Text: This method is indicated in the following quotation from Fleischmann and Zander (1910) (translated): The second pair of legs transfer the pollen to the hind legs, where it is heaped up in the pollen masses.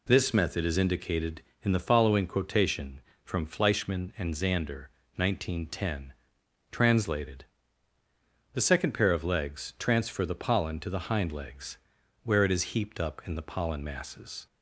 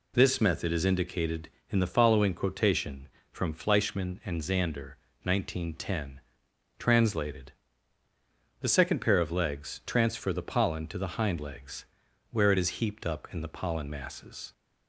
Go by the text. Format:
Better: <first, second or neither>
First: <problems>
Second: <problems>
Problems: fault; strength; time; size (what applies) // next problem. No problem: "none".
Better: neither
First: none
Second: none